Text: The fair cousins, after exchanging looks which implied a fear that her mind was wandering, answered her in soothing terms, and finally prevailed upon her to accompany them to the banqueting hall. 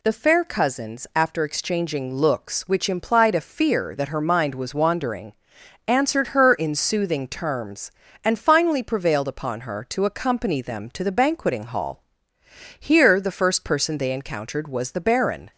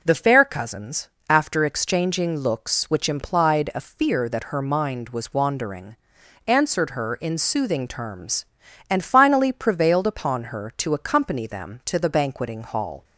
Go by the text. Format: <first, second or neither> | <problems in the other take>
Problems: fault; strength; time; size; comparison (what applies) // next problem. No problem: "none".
second | goes on to say "Here the first person they encountered was the Baron"; strong; from 12.7 s on; 2.7 s long